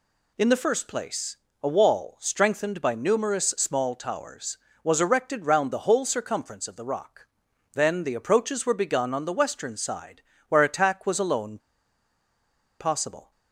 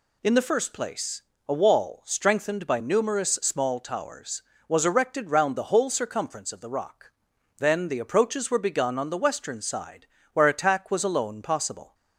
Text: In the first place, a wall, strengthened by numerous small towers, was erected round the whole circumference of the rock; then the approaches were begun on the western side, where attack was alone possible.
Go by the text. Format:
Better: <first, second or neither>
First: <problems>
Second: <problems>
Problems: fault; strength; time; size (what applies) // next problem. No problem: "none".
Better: second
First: pauses between "alone" and "possible"; at 11.5 s; 1.2 s long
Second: none